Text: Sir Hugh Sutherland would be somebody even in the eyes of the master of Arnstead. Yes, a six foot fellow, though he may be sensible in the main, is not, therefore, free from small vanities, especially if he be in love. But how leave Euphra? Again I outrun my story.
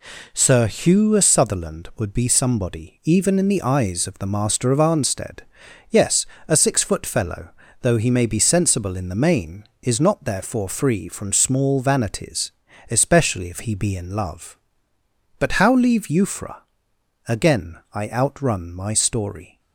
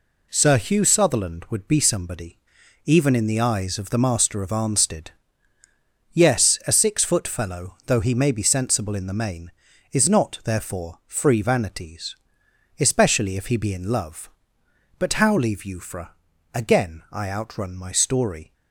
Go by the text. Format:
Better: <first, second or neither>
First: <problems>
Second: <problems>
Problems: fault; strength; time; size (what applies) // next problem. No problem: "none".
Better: first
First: none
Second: pauses between "somebody" and "even"; noticeable; at 2.3 s; 0.46 s long // skips "from small"; at 11.4 s